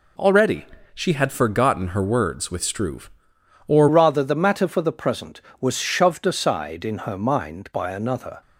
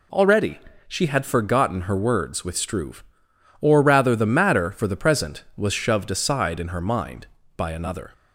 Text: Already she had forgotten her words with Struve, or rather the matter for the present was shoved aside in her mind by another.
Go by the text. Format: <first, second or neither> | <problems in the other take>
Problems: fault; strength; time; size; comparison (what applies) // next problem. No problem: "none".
second | pauses between "Already" and "she"; slight; at 0.6 s; 0.28 s long; slight in the second // changes voice at "rather"; from 3.8 s on; 4.6 s long